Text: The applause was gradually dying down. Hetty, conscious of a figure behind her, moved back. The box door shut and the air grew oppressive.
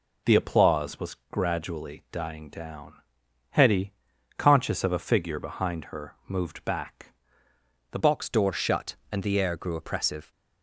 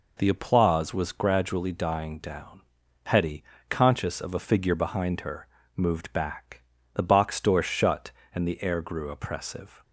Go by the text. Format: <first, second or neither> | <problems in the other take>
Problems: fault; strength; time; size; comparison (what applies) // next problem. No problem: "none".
second | pauses between "was" and "gradually"; slight; at 1.1 s; 0.16 s long // changes voice at "box"; from 8.0 s on; 2.3 s long